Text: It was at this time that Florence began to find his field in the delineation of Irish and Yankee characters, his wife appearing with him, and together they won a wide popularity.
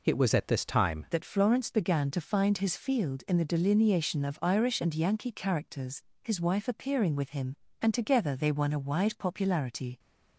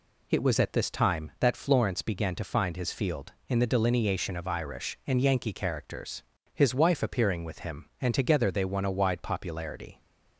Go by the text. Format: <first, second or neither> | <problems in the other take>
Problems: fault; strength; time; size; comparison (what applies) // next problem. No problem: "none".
second | changes voice at "that"; from 1.1 s on; 8.8 s long